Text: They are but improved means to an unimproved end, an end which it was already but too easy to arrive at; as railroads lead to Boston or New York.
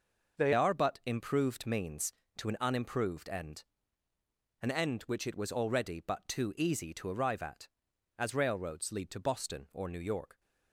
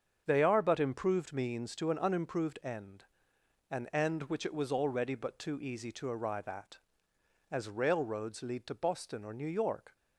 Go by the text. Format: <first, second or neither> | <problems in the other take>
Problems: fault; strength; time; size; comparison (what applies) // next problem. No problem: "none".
second | starts louder than the rest; noticeable; until 1.4 s; 6 dB; also in the second // changes voice at "are"; from 0.5 s on; 9.8 s long